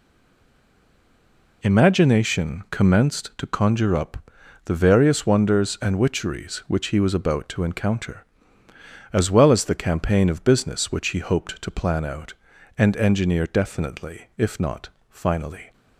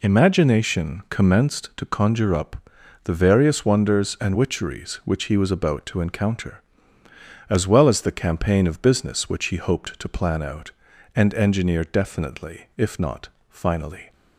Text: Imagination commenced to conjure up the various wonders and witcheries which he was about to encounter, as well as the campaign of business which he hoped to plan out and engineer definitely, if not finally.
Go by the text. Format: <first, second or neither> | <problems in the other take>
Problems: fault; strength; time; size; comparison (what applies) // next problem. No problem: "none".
second | stays silent before the first word; noticeable; until 1.6 s; 1.6 s long // pauses between "up" and "the"; noticeable; at 4.1 s; 0.48 s long; noticeable in the second // pauses between "not" and "finally"; slight; at 14.9 s; 0.20 s long; slight in the second